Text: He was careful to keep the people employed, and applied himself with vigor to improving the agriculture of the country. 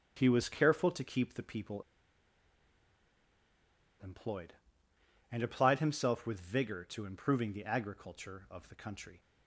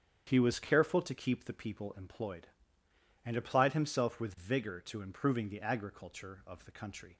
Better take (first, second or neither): second